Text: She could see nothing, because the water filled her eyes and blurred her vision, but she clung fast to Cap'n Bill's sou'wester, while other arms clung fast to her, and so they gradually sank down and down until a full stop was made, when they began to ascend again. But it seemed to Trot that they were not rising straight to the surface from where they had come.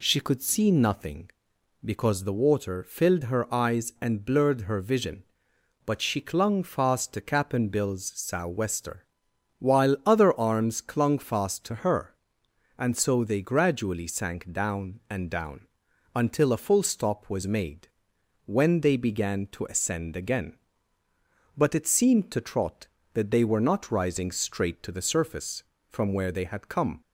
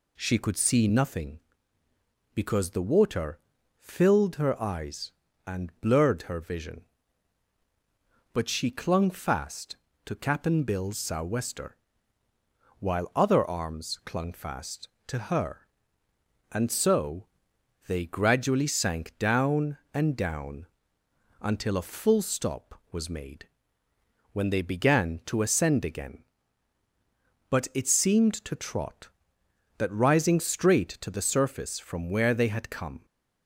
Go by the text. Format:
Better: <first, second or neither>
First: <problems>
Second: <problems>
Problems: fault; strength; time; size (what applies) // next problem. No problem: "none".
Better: first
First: pauses between "down" and "until"; noticeable; at 15.6 s; 0.48 s long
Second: pauses between "water" and "filled"; at 3.3 s; 0.40 s long // pauses between "so" and "they"; noticeable; at 17.2 s; 0.60 s long // pauses between "down" and "until"; noticeable; at 20.6 s; 0.76 s long // skips "they were not"; at 29.9 s